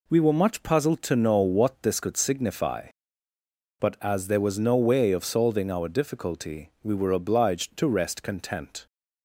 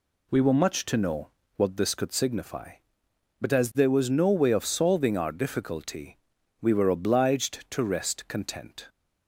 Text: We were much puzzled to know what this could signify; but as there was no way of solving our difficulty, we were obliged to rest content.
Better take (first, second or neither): first